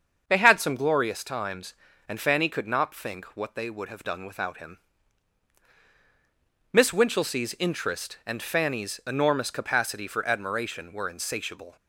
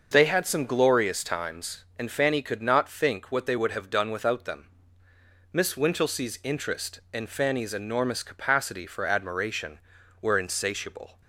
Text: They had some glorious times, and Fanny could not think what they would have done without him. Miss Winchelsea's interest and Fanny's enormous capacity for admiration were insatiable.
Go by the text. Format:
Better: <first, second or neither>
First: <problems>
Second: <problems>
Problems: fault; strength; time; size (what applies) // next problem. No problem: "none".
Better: first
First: starts louder than the rest; until 1.2 s; 6.5 dB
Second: starts louder than the rest; noticeable; until 1.1 s; 6 dB // says "them" for "him"; at 4.4 s